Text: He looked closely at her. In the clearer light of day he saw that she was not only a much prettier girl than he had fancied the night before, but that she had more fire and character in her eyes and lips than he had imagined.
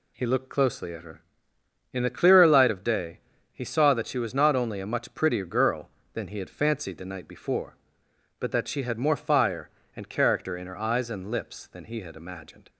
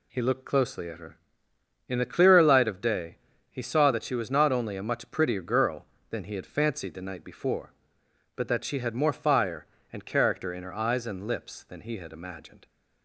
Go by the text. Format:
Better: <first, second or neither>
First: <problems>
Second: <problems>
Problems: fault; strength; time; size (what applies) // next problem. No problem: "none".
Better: neither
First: pauses between "day" and "he"; slight; at 3.1 s; 0.34 s long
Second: pauses between "day" and "he"; slight; at 3.1 s; 0.34 s long